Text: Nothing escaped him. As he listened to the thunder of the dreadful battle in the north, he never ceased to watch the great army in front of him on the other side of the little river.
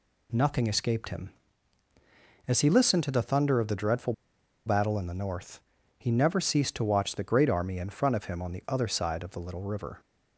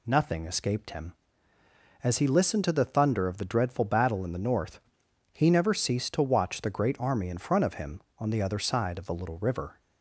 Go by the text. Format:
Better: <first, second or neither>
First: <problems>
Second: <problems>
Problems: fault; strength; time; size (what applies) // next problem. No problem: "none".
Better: second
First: pauses between "dreadful" and "battle"; noticeable; at 4.1 s; 0.53 s long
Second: none